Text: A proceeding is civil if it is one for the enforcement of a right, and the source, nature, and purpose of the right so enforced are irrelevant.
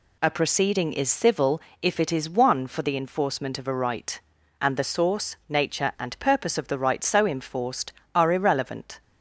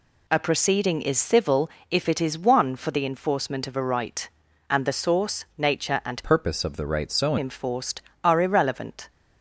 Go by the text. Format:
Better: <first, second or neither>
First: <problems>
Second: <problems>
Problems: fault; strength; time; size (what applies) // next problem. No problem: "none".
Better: first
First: pauses between "civil" and "if"; slight; at 1.6 s; 0.20 s long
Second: pauses between "civil" and "if"; slight; at 1.6 s; 0.20 s long // changes voice from "purpose" to "so"; from 6.2 to 7.3 s; 1.1 s long